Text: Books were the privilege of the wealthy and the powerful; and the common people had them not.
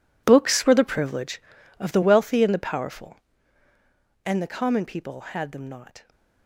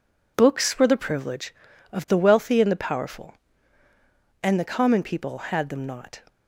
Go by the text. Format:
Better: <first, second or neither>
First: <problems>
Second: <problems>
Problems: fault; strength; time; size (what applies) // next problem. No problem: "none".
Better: second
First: gets quieter; strong; throughout; 15 dB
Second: none